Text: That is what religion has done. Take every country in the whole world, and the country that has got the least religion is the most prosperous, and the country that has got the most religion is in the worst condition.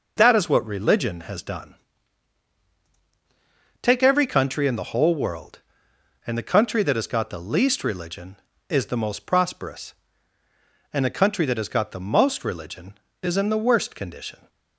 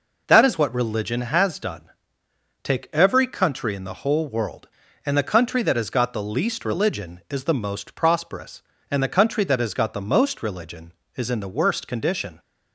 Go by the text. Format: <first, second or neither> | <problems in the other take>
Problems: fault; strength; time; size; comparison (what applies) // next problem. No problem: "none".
neither | none